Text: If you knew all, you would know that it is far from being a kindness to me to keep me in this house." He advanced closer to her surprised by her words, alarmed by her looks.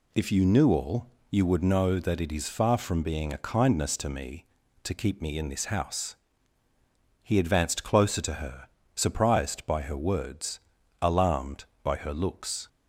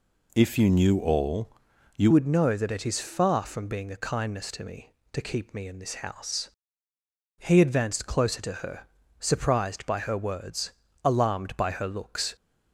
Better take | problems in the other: first | changes voice at "would"; from 2.1 s on; 10.2 s long // pauses between "her" and "surprised"; slight; at 8.8 s; 0.36 s long; slight in the first

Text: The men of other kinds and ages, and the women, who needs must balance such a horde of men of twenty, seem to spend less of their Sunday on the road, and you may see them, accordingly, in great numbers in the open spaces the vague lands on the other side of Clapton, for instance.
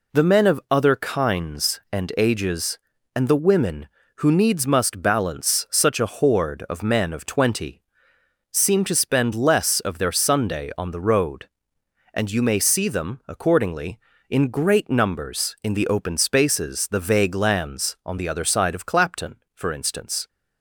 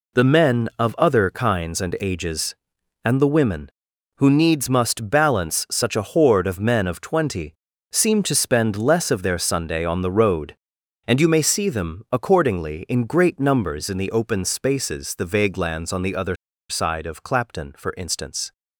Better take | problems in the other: first | pauses between "other" and "side"; slight; at 16.3 s; 0.34 s long

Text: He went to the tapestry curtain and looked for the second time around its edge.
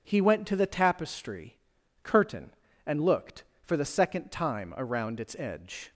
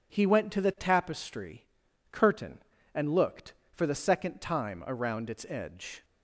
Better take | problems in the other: neither | pauses between "tapestry" and "curtain"; noticeable; the same in both

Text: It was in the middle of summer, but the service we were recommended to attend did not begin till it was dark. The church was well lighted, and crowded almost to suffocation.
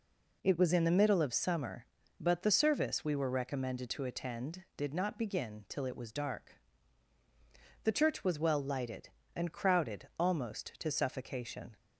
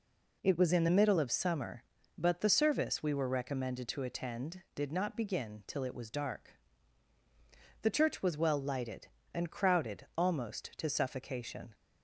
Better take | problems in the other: neither | none

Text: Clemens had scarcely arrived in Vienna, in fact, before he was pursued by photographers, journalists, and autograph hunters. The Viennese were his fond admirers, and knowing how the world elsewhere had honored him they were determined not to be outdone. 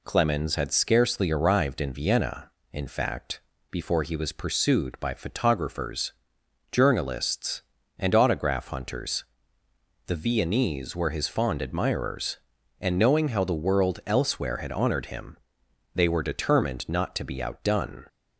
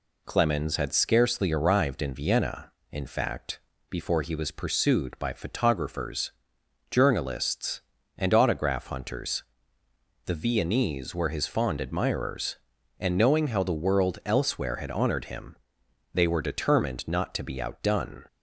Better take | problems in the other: neither | pauses between "him" and "they"; noticeable; the same in both

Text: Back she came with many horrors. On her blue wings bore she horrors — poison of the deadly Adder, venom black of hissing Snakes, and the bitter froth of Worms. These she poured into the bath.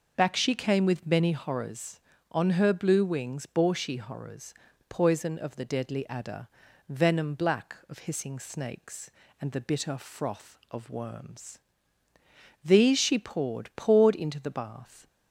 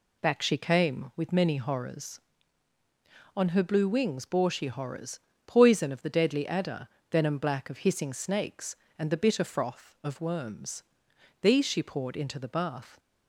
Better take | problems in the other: second | says "poured" twice; at 13.7 s

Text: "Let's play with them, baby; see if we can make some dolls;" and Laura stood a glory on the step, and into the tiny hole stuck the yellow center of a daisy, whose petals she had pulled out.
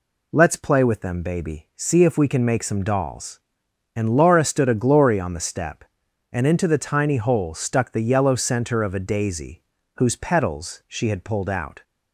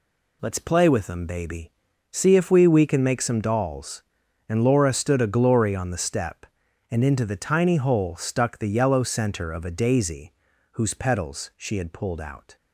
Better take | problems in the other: first | says "we" twice; at 2.6 s

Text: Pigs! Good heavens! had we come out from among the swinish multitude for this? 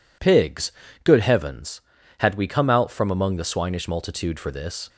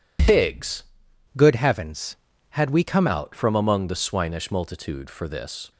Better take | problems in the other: first | changes voice from "Good" to "come"; from 1.3 to 3.0 s; 1.7 s long

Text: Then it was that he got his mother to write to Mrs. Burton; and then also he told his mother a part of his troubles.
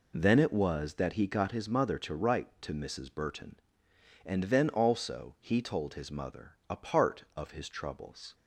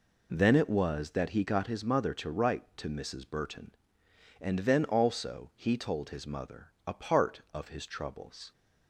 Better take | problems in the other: neither | none

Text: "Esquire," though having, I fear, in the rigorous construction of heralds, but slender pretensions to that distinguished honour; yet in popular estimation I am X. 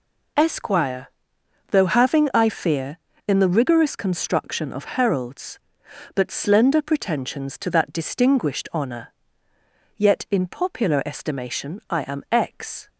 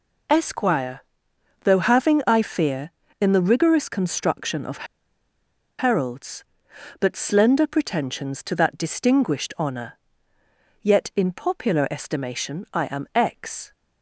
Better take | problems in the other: first | pauses between "of" and "heralds"; noticeable; at 4.8 s; 0.93 s long

